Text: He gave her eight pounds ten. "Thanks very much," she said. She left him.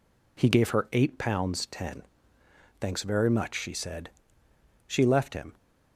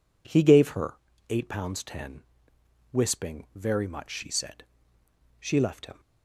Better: first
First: none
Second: pauses between "her" and "eight"; slight; at 0.9 s; 0.34 s long // says "Wisping" for "Thanks"; at 2.9 s

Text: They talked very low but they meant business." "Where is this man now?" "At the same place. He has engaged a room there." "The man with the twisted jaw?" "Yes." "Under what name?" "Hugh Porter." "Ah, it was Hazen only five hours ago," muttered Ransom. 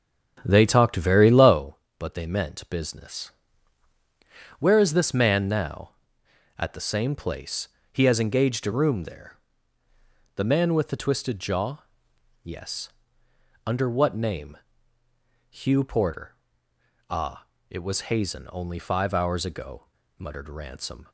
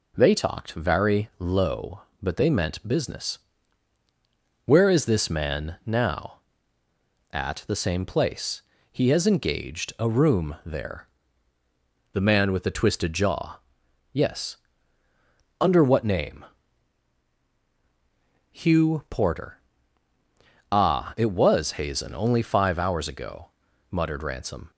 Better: second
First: starts louder than the rest; strong; until 1.6 s; 8 dB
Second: none

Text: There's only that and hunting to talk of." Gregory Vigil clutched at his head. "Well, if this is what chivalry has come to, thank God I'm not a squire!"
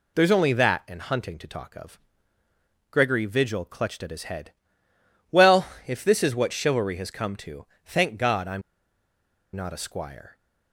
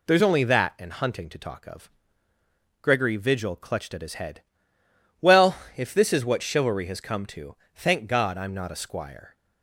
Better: second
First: pauses between "I'm" and "not"; noticeable; at 8.6 s; 0.93 s long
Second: none

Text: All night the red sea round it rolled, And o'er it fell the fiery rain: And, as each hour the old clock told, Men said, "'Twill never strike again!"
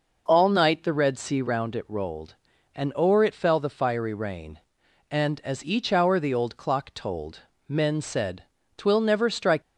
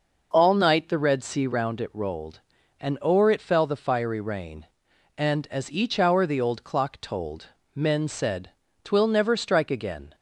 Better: second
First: stops before "again"; at 9.6 s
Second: none

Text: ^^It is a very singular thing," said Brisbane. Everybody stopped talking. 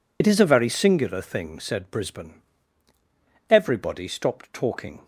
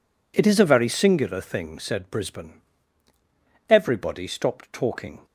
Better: second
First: loses the start of "It"; at 0.2 s; 60 ms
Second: none

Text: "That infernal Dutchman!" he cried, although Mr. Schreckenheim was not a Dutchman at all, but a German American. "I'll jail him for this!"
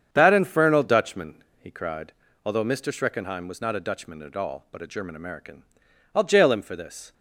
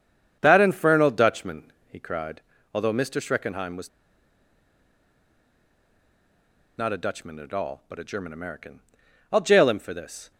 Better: first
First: starts louder than the rest; strong; until 1.1 s; 7.5 dB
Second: starts louder than the rest; strong; until 1.4 s; 8 dB // pauses between "was" and "not"; strong; at 3.8 s; 2.8 s long

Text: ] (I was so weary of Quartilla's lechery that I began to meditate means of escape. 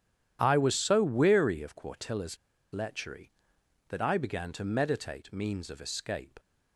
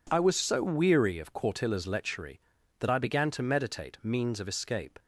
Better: second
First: starts louder than the rest; strong; until 1.4 s; 10.5 dB // pauses between "Quartilla's" and "lechery"; at 2.3 s; 0.36 s long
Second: none

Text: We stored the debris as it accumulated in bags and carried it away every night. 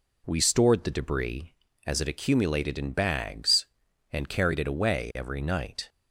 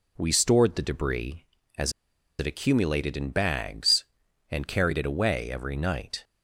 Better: first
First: none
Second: pauses between "as" and "it"; noticeable; at 1.9 s; 0.47 s long

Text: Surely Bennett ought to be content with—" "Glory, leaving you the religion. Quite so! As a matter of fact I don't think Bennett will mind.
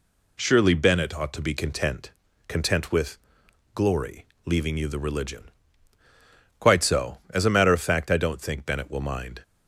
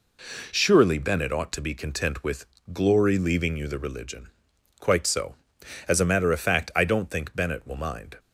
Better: second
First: says "content" twice; at 2.4 s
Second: none

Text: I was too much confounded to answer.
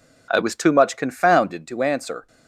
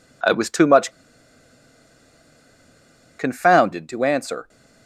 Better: first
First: none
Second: pauses between "much" and "confounded"; strong; at 0.9 s; 2.2 s long

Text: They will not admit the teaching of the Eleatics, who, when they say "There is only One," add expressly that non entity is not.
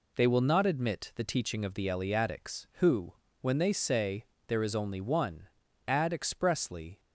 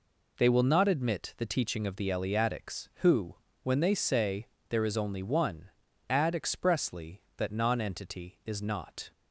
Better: second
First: pauses between "say" and "There"; slight; at 4.2 s; 0.22 s long // stops before "that non entity is not"; at 6.9 s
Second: pauses between "say" and "There"; slight; at 4.4 s; 0.22 s long

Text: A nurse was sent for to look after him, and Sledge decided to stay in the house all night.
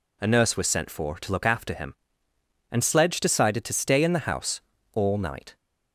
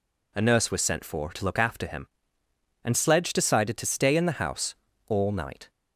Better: neither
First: pauses between "house" and "all"; slight; at 4.5 s; 0.34 s long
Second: pauses between "house" and "all"; slight; at 4.7 s; 0.34 s long

